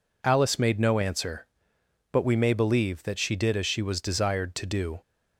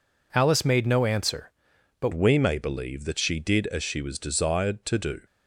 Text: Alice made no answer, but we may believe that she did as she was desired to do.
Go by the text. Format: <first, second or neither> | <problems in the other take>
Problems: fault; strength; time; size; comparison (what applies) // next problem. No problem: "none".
first | changes voice at "we"; from 2.1 s on; 3.1 s long